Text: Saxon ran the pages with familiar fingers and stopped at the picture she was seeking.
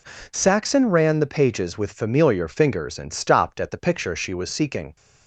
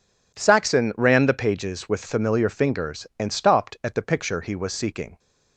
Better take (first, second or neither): first